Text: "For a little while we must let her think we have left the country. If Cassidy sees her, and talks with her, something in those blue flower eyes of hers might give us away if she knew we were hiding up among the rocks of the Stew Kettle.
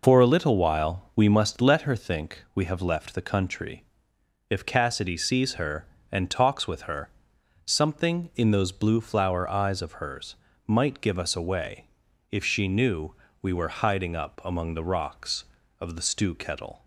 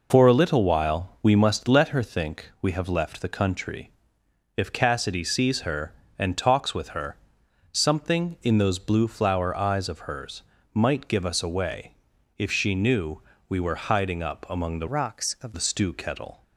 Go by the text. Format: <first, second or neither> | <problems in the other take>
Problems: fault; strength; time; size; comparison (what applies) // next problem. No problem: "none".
first | pauses between "hers" and "might"; slight; at 10.4 s; 0.32 s long; slight in the first // pauses between "away" and "if"; at 11.9 s; 0.42 s long; also in the first // pauses between "knew" and "we"; slight; at 13.2 s; 0.26 s long; slight in the first // changes voice from "rocks" to "of"; from 14.8 to 15.5 s; 0.7 s long